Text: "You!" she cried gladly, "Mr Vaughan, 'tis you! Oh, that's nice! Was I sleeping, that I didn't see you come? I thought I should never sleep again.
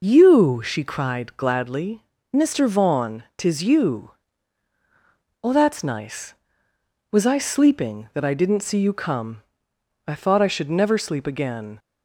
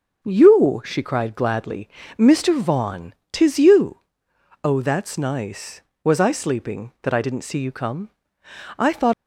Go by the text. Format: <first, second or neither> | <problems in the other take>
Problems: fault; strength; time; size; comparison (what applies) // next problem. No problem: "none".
first | stops before "I should never sleep again"; at 9.1 s